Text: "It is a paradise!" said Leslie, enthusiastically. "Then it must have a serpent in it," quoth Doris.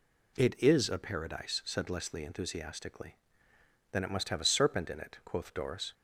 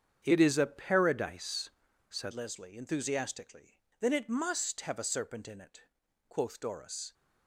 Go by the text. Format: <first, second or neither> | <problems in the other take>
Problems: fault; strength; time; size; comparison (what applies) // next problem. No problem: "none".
first | starts louder than the rest; strong; until 1.2 s; 7.5 dB // changes voice at "Leslie"; from 2.3 s on; 4.8 s long